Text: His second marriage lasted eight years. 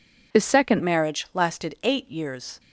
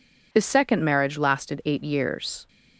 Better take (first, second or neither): second